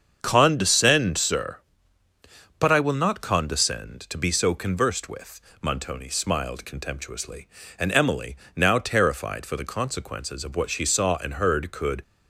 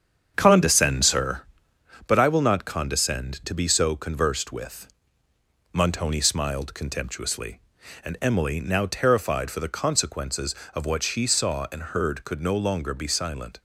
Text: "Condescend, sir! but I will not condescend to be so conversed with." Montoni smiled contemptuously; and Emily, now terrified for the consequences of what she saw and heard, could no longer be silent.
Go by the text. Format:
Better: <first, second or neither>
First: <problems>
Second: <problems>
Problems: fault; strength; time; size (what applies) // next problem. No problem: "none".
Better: second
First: starts louder than the rest; strong; until 1.2 s; 7 dB // stops before "no longer be silent"; at 12.0 s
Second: starts louder than the rest; strong; until 1.3 s; 7.5 dB